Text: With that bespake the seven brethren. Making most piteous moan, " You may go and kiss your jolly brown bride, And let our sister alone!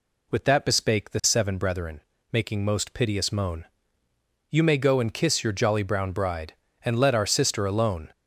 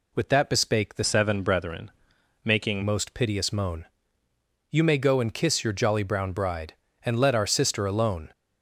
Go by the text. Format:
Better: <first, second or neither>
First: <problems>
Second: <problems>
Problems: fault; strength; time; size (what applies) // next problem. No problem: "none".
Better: first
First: none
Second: changes voice from "seven" to "Making"; from 1.0 to 2.8 s; 1.8 s long